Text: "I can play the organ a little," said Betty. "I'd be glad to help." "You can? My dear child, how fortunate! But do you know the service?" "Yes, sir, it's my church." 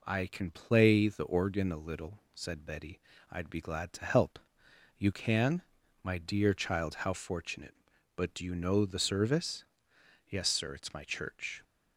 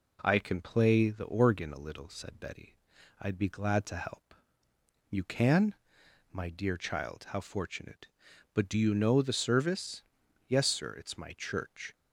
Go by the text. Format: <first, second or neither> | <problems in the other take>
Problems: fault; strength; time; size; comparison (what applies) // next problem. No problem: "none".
neither | none